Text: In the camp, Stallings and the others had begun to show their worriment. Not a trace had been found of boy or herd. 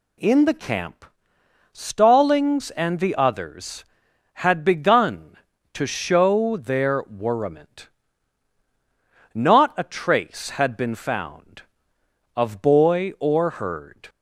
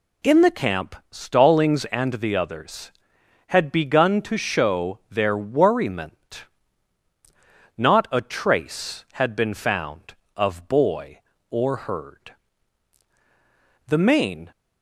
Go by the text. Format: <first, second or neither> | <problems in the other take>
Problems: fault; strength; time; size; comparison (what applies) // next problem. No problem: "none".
first | goes on to say "The main"; noticeable; from 13.8 s on; 0.64 s long